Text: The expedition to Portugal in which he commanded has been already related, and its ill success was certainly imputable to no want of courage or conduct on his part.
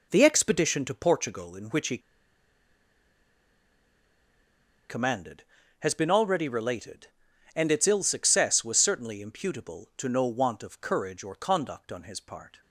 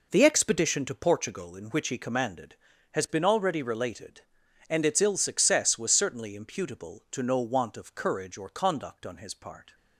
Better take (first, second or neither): second